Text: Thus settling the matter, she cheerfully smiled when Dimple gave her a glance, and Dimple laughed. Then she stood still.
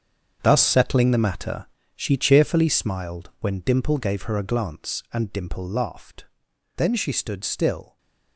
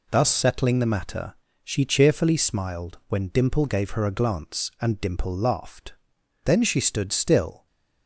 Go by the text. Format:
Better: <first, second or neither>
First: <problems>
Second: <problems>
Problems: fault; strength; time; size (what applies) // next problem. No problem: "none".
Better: second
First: gets quieter; strong; throughout; 12.5 dB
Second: none